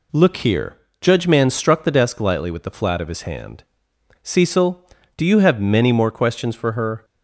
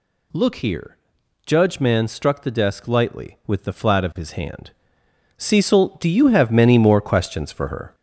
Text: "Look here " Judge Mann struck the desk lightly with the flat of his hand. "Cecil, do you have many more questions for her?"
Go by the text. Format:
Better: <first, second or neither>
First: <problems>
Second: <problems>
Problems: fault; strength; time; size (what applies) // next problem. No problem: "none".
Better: first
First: none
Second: gets louder; strong; throughout; 10.5 dB